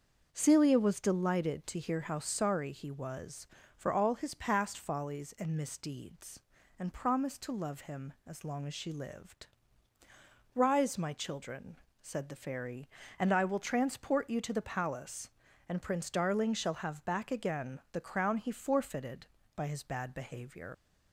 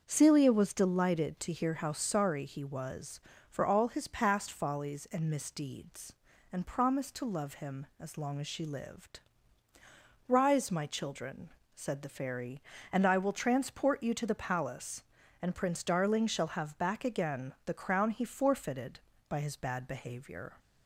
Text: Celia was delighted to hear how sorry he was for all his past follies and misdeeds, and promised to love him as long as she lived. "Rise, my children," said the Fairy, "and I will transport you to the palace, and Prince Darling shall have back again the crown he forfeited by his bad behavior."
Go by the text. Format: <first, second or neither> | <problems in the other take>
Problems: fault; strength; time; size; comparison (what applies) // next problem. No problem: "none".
second | starts louder than the rest; until 1.3 s; 6.5 dB; also in the second // leaves "behavior" unfinished; at 20.7 s; 105 ms